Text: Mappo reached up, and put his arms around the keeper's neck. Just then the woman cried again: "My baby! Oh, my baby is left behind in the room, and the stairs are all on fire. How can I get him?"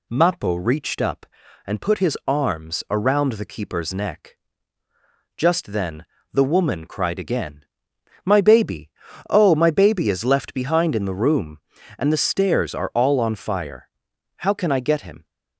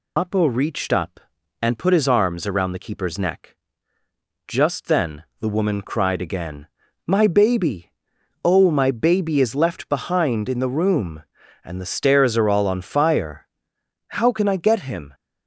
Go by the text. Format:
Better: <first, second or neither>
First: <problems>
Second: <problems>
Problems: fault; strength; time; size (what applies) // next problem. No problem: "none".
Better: first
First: pauses between "then" and "the"; slight; at 6.0 s; 0.26 s long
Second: loses the start of "Mappo"; at 0.1 s; 140 ms // pauses between "then" and "the"; slight; at 5.2 s; 0.16 s long